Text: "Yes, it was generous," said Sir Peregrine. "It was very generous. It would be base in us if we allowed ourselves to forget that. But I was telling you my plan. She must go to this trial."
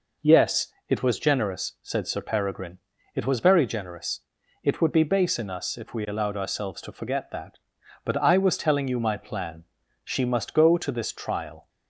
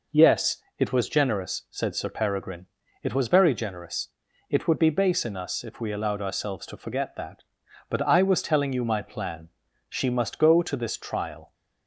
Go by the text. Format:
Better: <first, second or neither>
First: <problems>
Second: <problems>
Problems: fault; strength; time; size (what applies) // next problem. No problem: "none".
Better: neither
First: none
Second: none